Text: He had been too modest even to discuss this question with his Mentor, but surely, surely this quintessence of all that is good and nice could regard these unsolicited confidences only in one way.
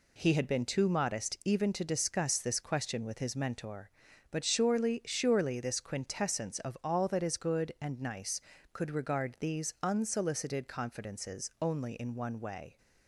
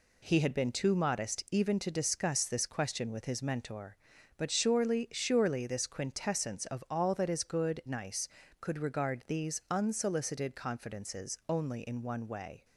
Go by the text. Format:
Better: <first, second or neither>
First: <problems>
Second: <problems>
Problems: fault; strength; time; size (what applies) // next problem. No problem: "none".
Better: first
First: none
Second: skips "and"; at 7.8 s